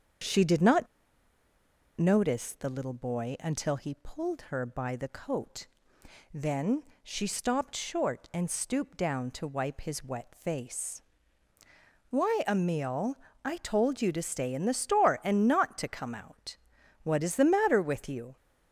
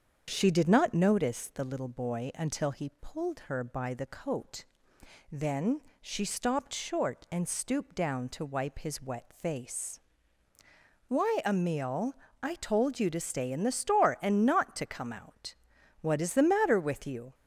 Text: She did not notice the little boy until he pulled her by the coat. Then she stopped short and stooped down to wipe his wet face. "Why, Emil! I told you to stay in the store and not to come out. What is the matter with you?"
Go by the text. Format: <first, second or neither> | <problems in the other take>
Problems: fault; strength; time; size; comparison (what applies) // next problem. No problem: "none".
second | starts louder than the rest; strong; until 2.3 s; 7.5 dB; strong in the second // pauses between "not" and "notice"; at 0.8 s; 1.1 s long // pauses between "Then" and "she"; slight; at 6.8 s; 0.18 s long; slight in the second